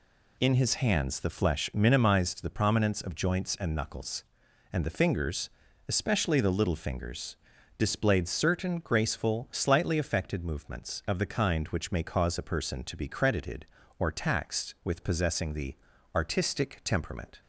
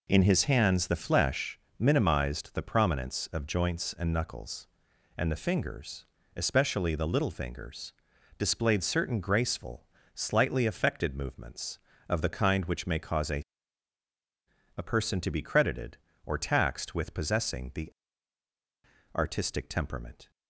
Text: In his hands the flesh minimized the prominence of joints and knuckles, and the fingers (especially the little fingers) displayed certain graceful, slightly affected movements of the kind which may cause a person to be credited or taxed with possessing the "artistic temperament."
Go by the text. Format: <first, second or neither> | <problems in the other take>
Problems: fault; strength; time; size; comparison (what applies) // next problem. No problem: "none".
first | pauses between "flesh" and "minimized"; slight; at 1.5 s; 0.20 s long // says "a" twice; at 14.7 s // pauses between "the" and "artistic"; at 17.9 s; 1.2 s long; also in the first